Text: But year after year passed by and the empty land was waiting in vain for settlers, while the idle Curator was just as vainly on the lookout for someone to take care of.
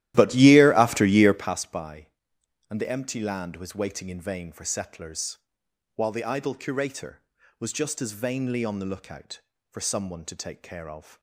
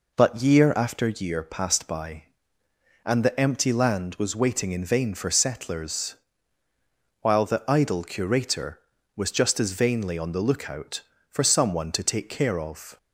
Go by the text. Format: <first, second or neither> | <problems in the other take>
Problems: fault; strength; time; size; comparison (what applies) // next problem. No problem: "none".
second | starts louder than the rest; strong; until 1.6 s; 13.5 dB